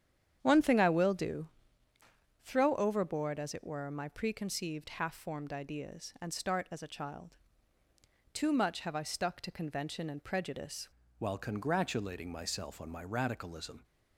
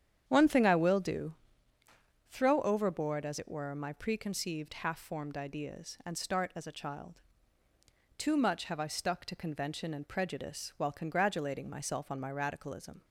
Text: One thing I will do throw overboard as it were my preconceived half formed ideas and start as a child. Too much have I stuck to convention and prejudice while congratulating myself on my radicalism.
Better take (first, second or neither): second